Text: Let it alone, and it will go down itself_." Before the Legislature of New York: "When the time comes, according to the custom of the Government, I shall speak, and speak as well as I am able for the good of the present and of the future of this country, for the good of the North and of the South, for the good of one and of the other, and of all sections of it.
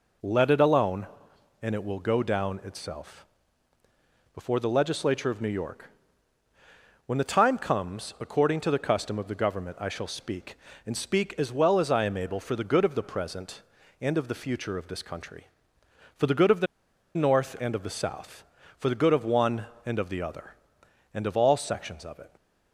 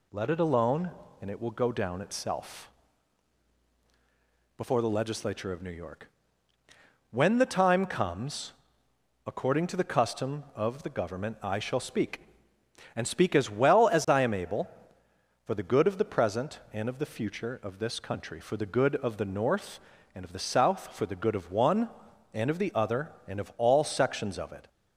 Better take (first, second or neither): second